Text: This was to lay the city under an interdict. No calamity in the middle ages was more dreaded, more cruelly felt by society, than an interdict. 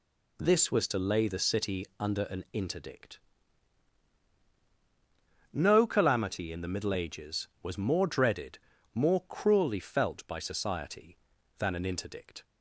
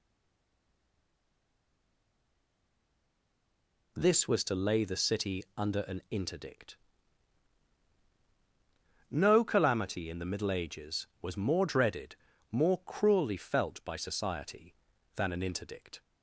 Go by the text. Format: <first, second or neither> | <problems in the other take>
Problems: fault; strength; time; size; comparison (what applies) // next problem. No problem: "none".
first | stays silent before the first word; strong; until 3.9 s; 3.9 s long